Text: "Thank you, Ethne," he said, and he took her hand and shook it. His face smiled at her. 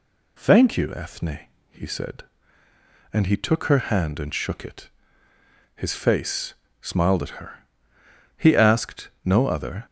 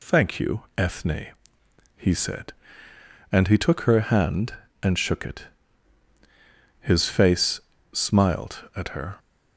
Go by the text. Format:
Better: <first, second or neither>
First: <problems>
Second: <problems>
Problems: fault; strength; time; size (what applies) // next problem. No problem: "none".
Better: second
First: pauses between "face" and "smiled"; slight; at 6.5 s; 0.28 s long // goes on to say "He asked no other"; from 8.3 s on; 1.4 s long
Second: pauses between "face" and "smiled"; slight; at 7.6 s; 0.32 s long